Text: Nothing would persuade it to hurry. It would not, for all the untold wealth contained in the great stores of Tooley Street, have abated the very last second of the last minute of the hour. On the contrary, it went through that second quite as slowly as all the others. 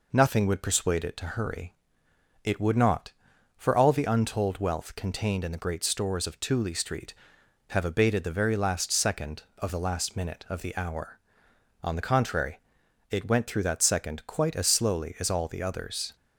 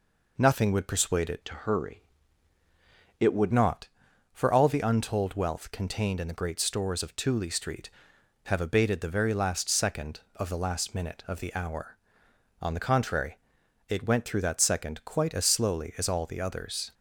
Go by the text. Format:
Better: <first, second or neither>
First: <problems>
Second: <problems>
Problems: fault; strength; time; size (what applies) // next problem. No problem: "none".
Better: first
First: none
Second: changes voice from "to" to "would"; from 1.4 to 3.5 s; 2.1 s long